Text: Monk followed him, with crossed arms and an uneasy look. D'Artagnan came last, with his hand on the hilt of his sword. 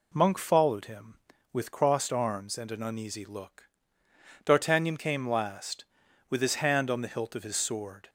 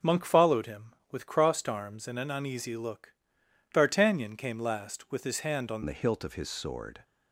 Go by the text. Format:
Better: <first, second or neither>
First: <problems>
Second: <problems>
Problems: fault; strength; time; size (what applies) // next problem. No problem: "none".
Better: first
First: none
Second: changes voice at "the"; from 5.8 s on; 1.2 s long